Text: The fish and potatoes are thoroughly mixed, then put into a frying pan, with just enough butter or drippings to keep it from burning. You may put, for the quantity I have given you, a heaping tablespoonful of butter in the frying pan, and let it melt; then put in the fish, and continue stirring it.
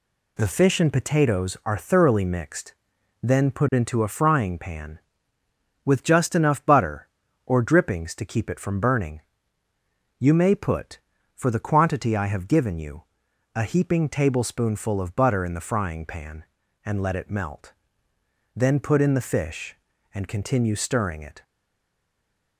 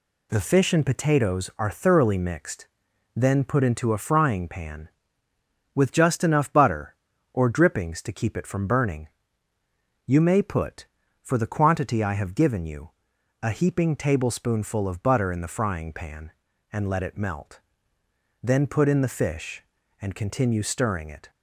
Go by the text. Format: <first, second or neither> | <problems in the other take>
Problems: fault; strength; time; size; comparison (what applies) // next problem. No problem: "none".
second | stays silent after the last word; noticeable; from 21.4 s on; 1.1 s long